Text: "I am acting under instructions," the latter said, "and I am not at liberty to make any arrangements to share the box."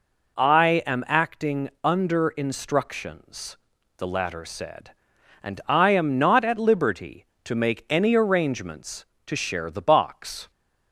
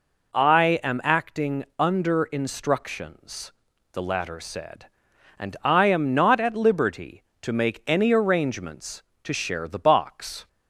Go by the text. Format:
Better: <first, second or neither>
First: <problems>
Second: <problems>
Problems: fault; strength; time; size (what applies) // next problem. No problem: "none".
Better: neither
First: none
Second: none